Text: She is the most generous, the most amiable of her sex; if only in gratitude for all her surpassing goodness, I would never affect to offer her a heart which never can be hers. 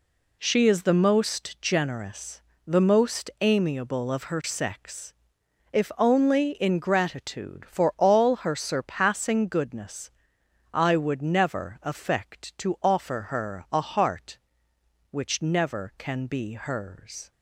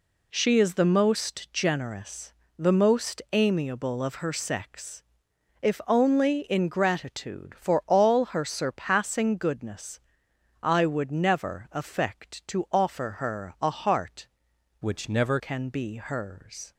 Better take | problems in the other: first | changes voice from "which" to "never"; from 14.8 to 15.3 s; 0.5 s long

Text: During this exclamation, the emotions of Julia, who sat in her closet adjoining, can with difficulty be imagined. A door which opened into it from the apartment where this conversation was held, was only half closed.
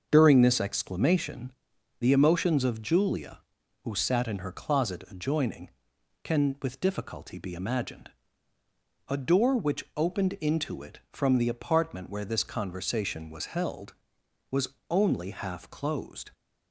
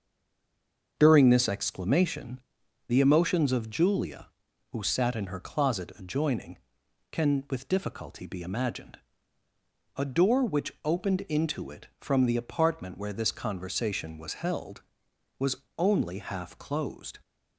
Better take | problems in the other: first | stays silent before the first word; until 0.9 s; 0.9 s long // starts louder than the rest; until 1.9 s; 6.5 dB; also in the first // pauses between "was" and "only"; slight; at 15.5 s; 0.20 s long; slight in the first

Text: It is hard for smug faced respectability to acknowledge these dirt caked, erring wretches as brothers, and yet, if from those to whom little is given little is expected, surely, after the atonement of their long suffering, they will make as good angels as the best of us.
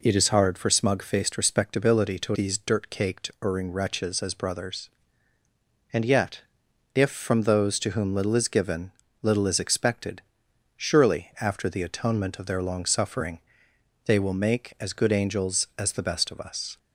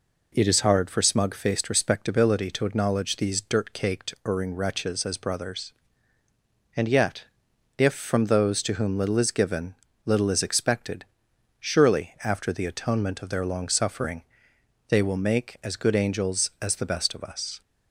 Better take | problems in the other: second | skips "acknowledge"; at 2.3 s // pauses between "given" and "little"; slight; at 8.9 s; 0.30 s long; slight in the second

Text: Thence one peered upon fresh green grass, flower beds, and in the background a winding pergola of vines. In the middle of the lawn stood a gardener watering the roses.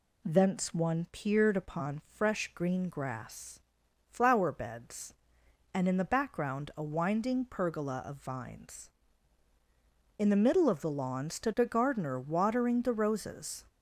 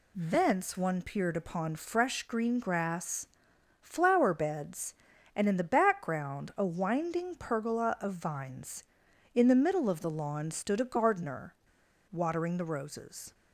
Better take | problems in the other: first | pauses between "gardener" and "watering"; noticeable; at 11.5 s; 0.56 s long

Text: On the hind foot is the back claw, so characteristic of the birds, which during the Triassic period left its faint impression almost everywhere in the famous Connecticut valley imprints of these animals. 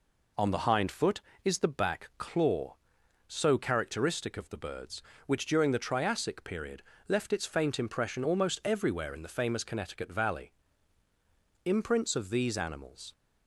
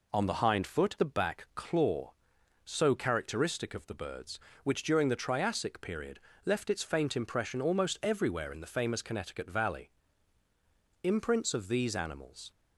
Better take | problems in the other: first | skips "is"; at 0.9 s // pauses between "period" and "left"; slight; at 6.1 s; 0.24 s long; slight in the first // pauses between "valley" and "imprints"; at 9.8 s; 1.1 s long; also in the first

